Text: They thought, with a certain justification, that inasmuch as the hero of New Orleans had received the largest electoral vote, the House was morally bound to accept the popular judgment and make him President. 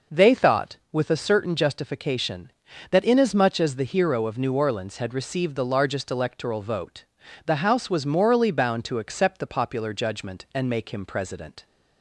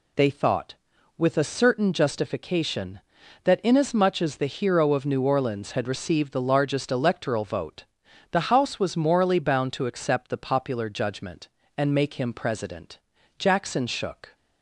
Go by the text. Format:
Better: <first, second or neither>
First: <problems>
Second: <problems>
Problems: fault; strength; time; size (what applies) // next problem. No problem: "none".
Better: first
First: none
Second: goes on to say "Jackson shook"; noticeable; from 13.3 s on; 0.96 s long